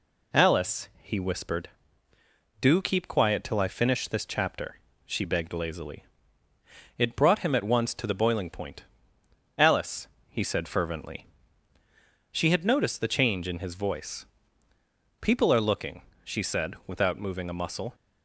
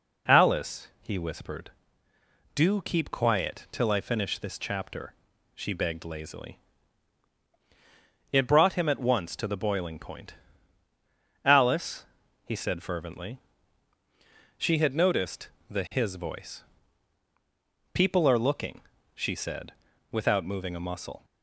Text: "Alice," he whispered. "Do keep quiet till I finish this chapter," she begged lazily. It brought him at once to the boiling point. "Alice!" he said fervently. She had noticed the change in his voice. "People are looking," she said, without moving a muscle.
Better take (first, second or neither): first